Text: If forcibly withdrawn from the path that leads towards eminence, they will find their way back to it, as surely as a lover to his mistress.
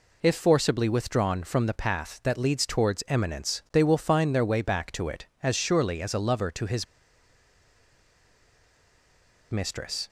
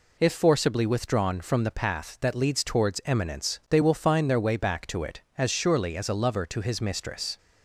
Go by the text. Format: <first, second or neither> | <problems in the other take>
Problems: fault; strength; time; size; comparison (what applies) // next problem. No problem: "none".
second | pauses between "his" and "mistress"; strong; at 6.8 s; 2.6 s long